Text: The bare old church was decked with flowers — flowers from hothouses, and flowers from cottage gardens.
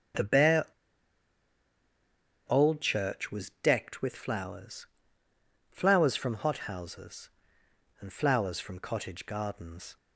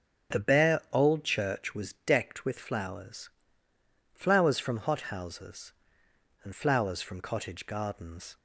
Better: second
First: starts louder than the rest; strong; until 3.0 s; 8.5 dB // pauses between "bare" and "old"; strong; at 0.6 s; 1.8 s long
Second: starts louder than the rest; strong; until 1.4 s; 8.5 dB

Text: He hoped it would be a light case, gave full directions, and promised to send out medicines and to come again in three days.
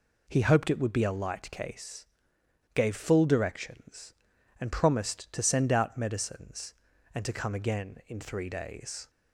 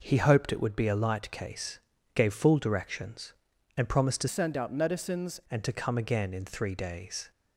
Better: first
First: none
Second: changes voice from "send" to "medicines"; from 4.2 to 5.4 s; 1.2 s long

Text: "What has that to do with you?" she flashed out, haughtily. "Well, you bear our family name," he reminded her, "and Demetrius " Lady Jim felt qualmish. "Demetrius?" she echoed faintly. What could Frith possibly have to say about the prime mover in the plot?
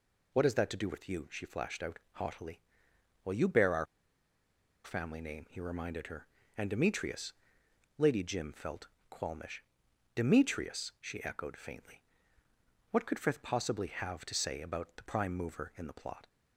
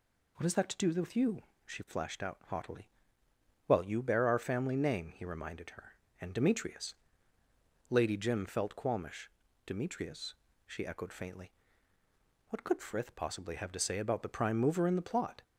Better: second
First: pauses between "our" and "family"; at 3.8 s; 0.99 s long // pauses between "felt" and "qualmish"; slight; at 8.8 s; 0.22 s long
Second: none

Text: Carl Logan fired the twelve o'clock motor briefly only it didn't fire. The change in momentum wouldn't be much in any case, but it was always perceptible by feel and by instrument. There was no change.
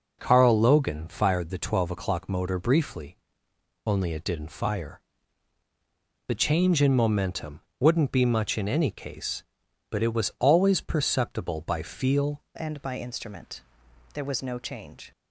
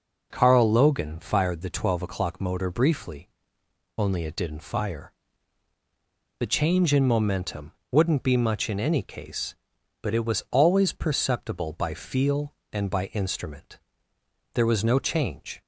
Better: second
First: pauses between "briefly" and "only"; noticeable; at 3.1 s; 0.70 s long // pauses between "momentum" and "wouldn't"; slight; at 7.5 s; 0.20 s long // changes voice at "and"; from 12.5 s on; 2.6 s long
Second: pauses between "briefly" and "only"; noticeable; at 3.2 s; 0.70 s long // pauses between "momentum" and "wouldn't"; slight; at 7.7 s; 0.20 s long

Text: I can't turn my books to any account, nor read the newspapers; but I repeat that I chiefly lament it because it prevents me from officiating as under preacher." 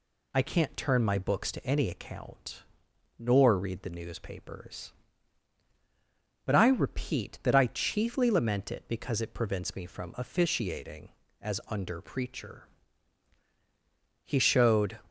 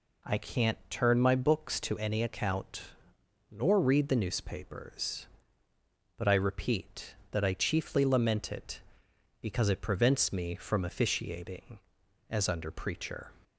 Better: second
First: goes on to say "He showed"; noticeable; from 14.2 s on; 0.76 s long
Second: none

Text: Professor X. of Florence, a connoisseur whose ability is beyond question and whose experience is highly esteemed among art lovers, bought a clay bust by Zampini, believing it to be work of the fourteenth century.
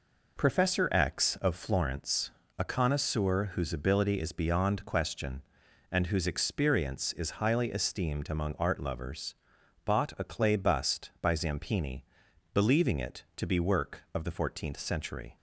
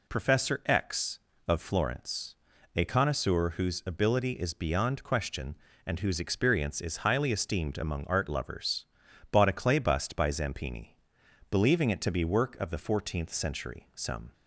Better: first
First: none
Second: goes on to say "Some"; slight; from 13.9 s on; 0.38 s long

